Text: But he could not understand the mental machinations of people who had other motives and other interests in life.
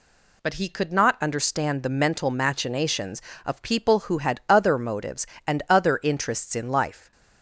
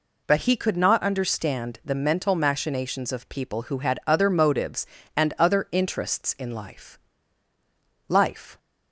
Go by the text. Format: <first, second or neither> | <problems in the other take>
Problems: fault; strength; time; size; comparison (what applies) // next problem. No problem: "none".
first | says "life" twice; at 8.0 s